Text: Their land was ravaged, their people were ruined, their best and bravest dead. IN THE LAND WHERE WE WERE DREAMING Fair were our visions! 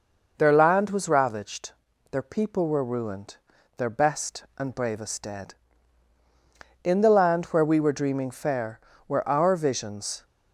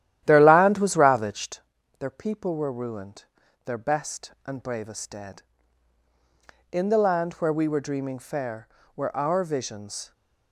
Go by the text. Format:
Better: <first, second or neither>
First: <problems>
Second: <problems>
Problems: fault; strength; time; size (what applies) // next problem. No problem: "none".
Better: first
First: none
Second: starts louder than the rest; strong; until 1.6 s; 12 dB